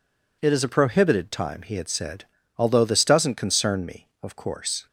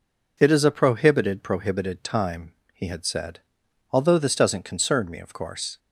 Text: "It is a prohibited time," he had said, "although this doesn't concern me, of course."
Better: first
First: none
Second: says "prohibited" twice; at 1.4 s

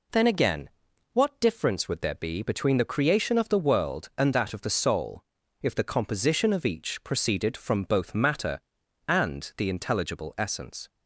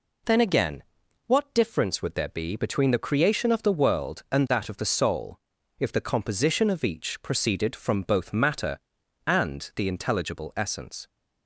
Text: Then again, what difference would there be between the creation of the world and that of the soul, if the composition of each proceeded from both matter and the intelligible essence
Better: neither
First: none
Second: none

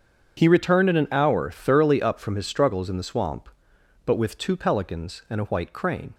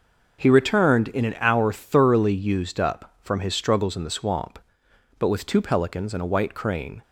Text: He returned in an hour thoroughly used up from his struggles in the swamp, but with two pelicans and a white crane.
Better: second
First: starts louder than the rest; strong; until 1.3 s; 7.5 dB // skips "used"; at 2.0 s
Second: none

